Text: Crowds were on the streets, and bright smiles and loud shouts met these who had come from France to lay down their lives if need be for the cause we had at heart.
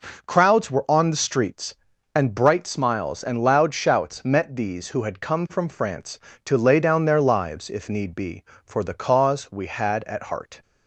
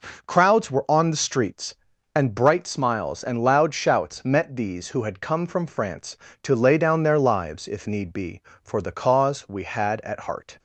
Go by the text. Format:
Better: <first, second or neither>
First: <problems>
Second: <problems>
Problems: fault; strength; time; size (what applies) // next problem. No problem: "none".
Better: neither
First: none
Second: none